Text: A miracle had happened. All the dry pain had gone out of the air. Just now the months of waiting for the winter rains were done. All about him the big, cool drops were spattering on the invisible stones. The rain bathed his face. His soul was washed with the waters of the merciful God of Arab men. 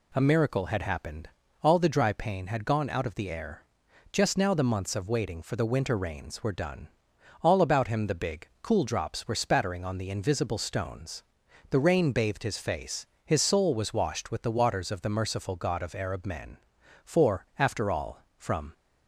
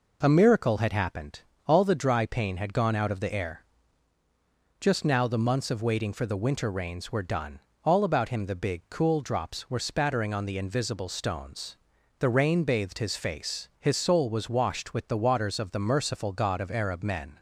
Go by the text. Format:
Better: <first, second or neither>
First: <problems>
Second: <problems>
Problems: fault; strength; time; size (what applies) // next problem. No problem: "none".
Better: second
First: goes on to say "For after all from"; from 17.0 s on; 1.6 s long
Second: none